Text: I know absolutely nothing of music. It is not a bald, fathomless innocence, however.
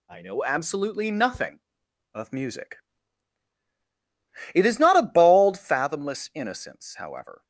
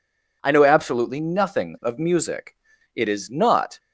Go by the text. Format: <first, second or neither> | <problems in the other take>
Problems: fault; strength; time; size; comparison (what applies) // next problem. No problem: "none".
first | stops before "a bald fathomless innocence however"; at 3.7 s